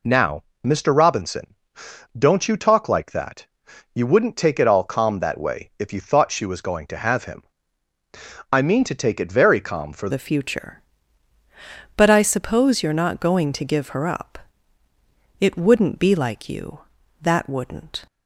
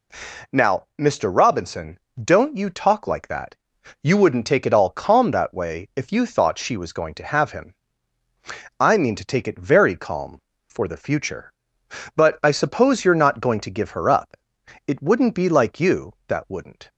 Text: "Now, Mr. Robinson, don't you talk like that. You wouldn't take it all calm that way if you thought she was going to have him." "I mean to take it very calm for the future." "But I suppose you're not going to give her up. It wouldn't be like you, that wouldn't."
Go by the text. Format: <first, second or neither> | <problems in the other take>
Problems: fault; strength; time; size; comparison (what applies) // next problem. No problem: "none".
second | changes voice at "the"; from 10.0 s on; 8.0 s long